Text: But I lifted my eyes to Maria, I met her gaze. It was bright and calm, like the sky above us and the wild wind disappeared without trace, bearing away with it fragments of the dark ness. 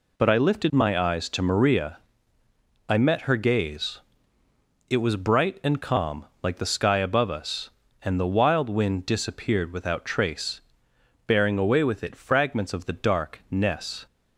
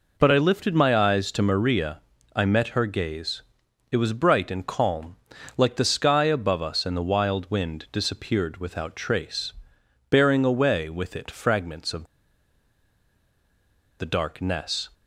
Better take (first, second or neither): first